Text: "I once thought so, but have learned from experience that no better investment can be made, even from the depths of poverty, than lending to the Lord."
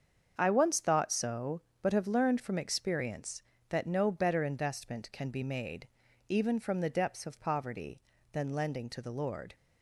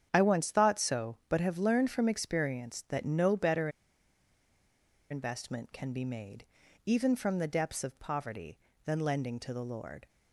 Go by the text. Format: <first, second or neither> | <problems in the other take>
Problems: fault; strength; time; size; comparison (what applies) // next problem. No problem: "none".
first | starts louder than the rest; strong; until 1.1 s; 8.5 dB; strong in the first // pauses between "better" and "investment"; strong; at 3.6 s; 1.4 s long